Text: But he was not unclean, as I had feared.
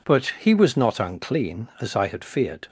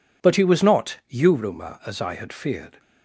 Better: first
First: none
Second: says "yuruma" for "unclean"; at 1.0 s

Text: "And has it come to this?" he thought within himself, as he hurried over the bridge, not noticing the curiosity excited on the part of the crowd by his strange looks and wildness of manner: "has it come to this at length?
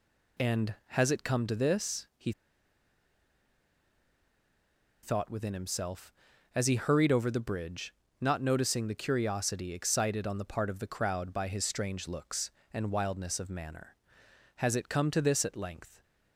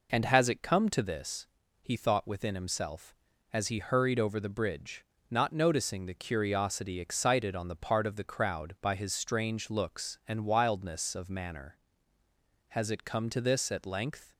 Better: second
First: pauses between "he" and "thought"; strong; at 2.3 s; 2.7 s long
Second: none

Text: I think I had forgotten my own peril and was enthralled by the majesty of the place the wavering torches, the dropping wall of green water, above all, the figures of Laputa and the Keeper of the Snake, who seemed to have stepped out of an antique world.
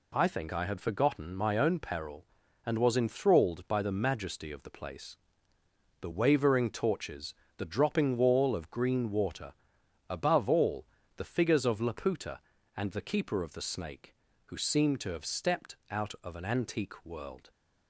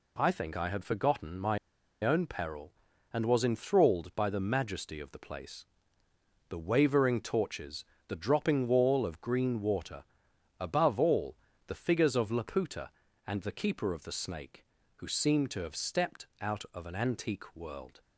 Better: first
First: pauses between "place" and "the"; noticeable; at 5.1 s; 0.86 s long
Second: pauses between "my" and "own"; noticeable; at 1.5 s; 0.46 s long // pauses between "place" and "the"; noticeable; at 5.6 s; 0.86 s long

